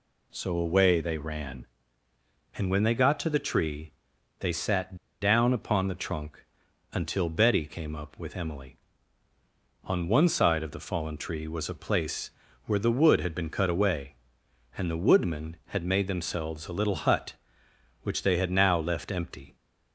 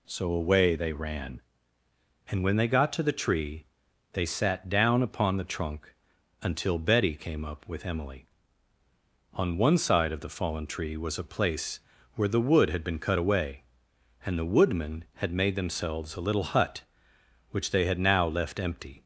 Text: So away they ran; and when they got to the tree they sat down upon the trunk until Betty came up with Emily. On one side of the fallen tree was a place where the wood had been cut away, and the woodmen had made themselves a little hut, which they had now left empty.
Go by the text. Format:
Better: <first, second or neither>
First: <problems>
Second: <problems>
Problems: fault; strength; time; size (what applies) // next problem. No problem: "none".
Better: second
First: pauses between "tree" and "they"; noticeable; at 3.9 s; 0.48 s long // pauses between "sat" and "down"; slight; at 4.9 s; 0.26 s long // pauses between "trunk" and "until"; noticeable; at 6.4 s; 0.48 s long // pauses between "place" and "where"; slight; at 12.3 s; 0.36 s long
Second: pauses between "tree" and "they"; noticeable; at 3.6 s; 0.48 s long // pauses between "trunk" and "until"; noticeable; at 5.9 s; 0.48 s long // pauses between "place" and "where"; slight; at 11.8 s; 0.36 s long